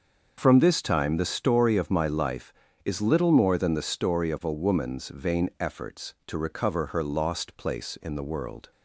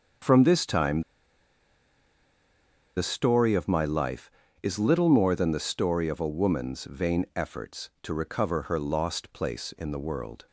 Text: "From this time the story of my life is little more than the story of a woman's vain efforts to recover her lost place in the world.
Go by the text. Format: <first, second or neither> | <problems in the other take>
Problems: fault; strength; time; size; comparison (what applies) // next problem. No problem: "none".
first | starts louder than the rest; until 3.1 s; 6.5 dB; also in the first // pauses between "time" and "the"; strong; at 1.0 s; 1.9 s long